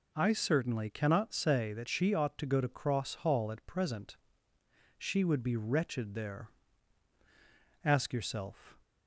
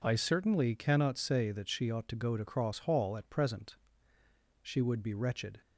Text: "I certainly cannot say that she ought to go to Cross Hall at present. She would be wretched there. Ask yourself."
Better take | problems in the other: first | stops before "there Ask yourself"; at 5.6 s

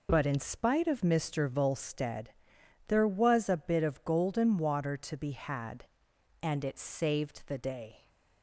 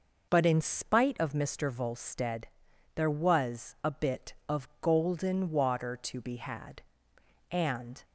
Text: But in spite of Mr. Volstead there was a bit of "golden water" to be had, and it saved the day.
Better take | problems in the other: first | pauses between "Volstead" and "there"; noticeable; at 2.4 s; 0.48 s long; noticeable in the first // stops before "it saved the day"; at 8.0 s

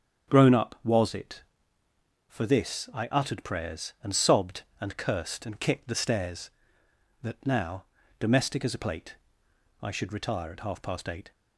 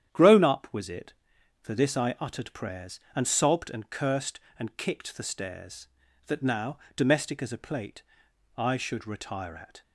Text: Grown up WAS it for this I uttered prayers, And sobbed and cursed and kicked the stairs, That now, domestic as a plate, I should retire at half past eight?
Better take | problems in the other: first | starts louder than the rest; strong; until 1.6 s; 10 dB; strong in the first // stops before "half past eight"; at 9.8 s

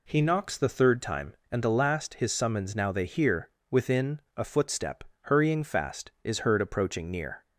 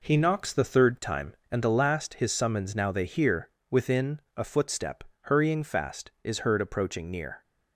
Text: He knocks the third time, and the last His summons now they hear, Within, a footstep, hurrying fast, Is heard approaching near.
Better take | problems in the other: first | gets quieter; strong; throughout; 7 dB

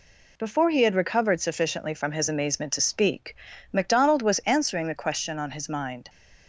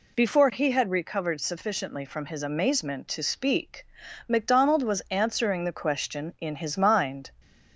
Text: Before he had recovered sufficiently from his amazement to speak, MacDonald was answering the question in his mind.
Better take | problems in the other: second | says "on" for "in"; at 5.3 s

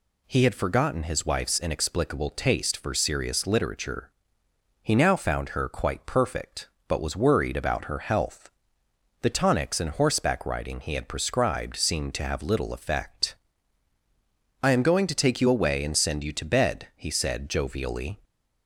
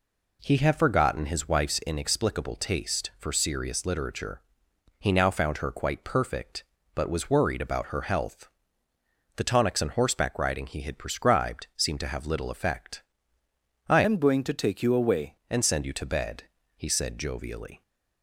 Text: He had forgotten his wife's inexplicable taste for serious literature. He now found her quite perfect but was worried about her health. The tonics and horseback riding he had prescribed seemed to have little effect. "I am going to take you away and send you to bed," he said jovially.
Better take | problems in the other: first | changes voice from "am" to "away"; from 14.0 to 15.3 s; 1.3 s long

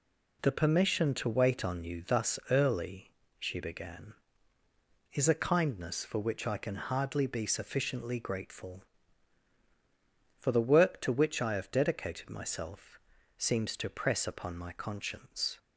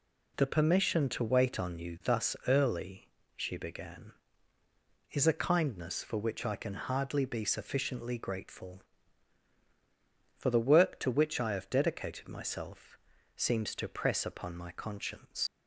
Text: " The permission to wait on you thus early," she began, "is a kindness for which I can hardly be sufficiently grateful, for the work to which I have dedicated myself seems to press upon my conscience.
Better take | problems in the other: first | pauses between "myself" and "seems"; slight; at 12.9 s; 0.36 s long; slight in the first // leaves "conscience" unfinished; at 15.4 s; 105 ms

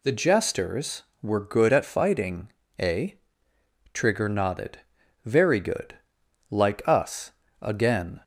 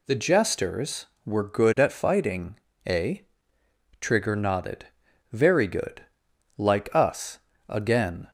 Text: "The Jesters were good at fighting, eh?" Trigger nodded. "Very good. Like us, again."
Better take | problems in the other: neither | none

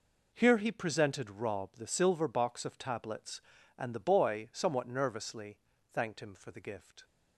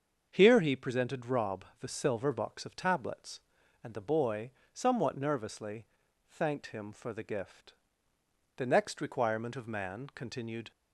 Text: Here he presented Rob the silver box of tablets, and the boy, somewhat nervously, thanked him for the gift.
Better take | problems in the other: first | starts louder than the rest; until 1.3 s; 6.5 dB // pauses between "Rob" and "the"; slight; at 1.6 s; 0.16 s long // goes on to say "The next requirement of man continued"; strong; from 8.5 s on; 2.1 s long

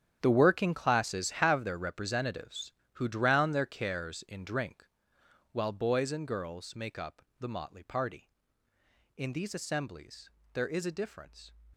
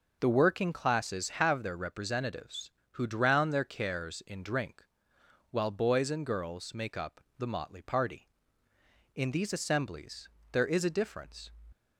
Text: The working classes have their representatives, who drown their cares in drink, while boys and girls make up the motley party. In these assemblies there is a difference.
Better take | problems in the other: second | gets quieter; strong; throughout; 14 dB // pauses between "up" and "the"; slight; at 7.2 s; 0.18 s long; slight in the second // pauses between "assemblies" and "there"; slight; at 10.2 s; 0.22 s long; slight in the second

